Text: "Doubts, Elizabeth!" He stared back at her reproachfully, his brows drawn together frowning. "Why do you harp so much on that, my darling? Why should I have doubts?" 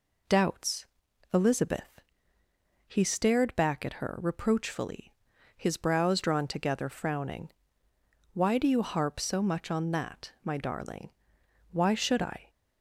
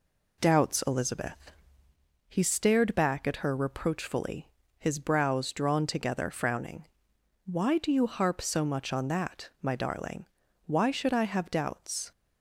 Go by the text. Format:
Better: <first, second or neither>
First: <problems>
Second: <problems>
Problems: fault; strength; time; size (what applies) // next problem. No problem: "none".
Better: second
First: stops before "have doubts"; at 12.4 s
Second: none